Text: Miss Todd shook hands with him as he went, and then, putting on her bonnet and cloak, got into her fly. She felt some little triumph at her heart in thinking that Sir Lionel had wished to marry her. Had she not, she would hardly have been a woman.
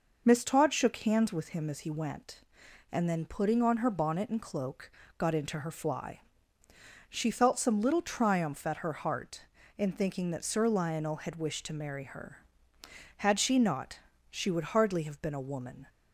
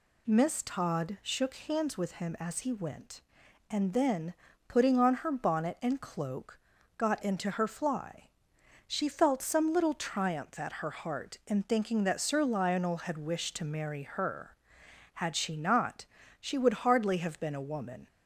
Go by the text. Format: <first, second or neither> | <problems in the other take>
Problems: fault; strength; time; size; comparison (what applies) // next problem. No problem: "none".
neither | none